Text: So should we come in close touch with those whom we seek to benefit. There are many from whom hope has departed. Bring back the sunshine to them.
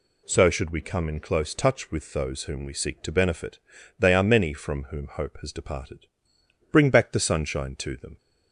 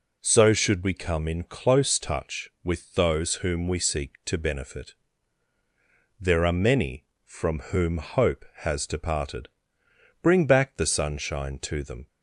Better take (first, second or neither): second